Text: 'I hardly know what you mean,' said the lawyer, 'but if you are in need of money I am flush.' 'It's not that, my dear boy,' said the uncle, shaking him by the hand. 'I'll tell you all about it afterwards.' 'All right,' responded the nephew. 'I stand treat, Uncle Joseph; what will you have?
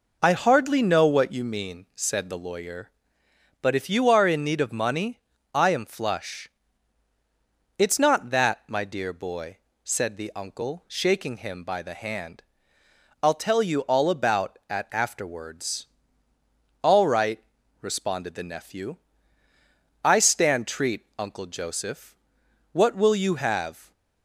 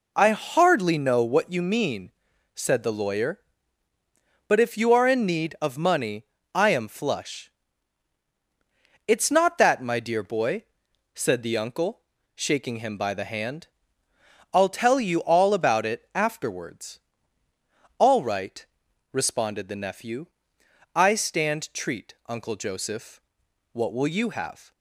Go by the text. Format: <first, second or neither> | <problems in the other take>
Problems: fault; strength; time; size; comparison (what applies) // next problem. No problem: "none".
second | pauses between "money" and "I"; slight; at 5.2 s; 0.34 s long; slight in the second // says "at" for "it"; at 14.6 s